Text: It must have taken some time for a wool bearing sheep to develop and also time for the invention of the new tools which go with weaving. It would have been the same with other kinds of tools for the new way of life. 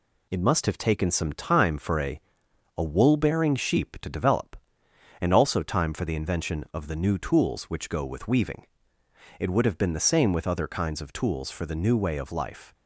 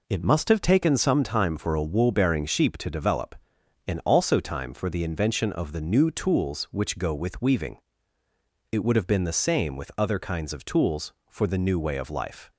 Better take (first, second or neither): second